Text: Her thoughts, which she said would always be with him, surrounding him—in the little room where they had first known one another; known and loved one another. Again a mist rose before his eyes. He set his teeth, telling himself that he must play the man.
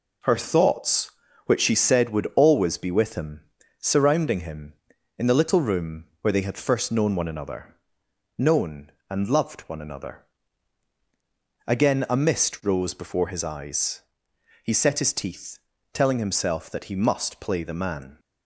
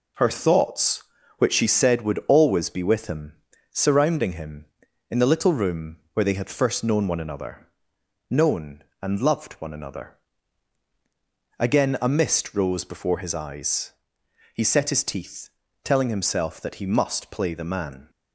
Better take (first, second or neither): neither